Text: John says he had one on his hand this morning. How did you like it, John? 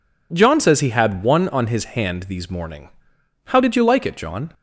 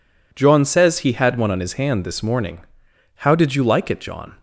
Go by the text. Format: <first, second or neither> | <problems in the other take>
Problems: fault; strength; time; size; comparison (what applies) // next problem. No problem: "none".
second | says "these" for "this"; at 2.2 s